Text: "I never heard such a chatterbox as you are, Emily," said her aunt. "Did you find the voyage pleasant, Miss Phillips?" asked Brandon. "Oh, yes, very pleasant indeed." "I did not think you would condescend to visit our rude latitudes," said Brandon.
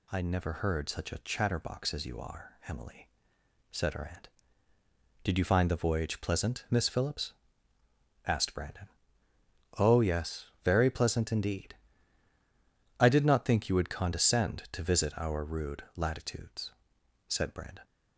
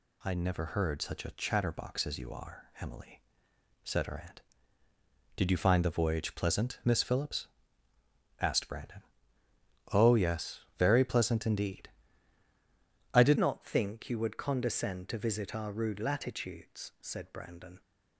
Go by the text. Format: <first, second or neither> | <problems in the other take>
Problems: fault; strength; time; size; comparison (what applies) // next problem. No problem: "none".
first | changes voice at "not"; from 13.3 s on; 4.5 s long